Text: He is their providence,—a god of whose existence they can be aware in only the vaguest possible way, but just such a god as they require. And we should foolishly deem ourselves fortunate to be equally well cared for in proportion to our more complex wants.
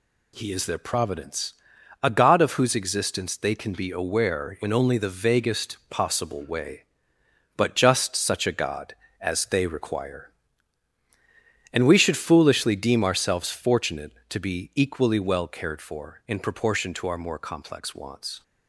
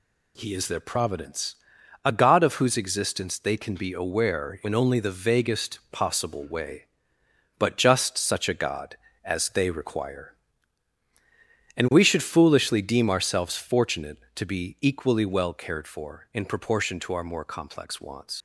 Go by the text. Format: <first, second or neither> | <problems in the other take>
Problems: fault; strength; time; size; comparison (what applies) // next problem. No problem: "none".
first | leaves "wants" unfinished; at 18.3 s; 80 ms